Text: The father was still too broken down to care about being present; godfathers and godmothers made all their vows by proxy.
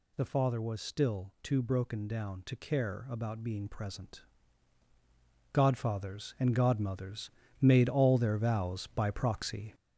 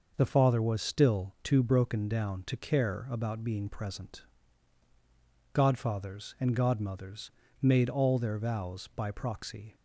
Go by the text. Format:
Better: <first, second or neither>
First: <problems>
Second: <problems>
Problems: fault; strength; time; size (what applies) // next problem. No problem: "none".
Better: second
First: gets louder; noticeable; throughout; 4.5 dB // pauses between "godmothers" and "made"; slight; at 7.3 s; 0.30 s long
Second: pauses between "godmothers" and "made"; slight; at 7.3 s; 0.30 s long